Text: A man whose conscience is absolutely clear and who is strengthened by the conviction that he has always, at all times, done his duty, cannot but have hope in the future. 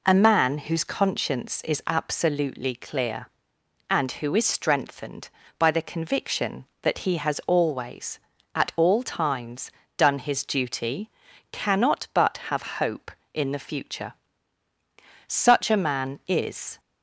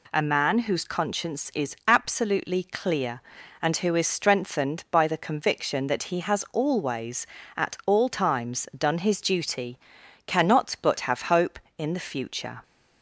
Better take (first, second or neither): second